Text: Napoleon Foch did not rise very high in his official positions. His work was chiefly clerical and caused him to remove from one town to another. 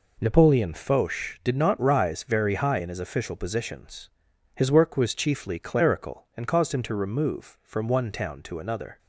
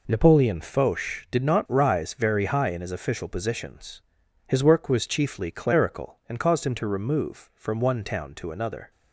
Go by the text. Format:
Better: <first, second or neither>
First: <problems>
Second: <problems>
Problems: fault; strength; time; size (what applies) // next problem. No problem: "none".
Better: neither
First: none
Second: none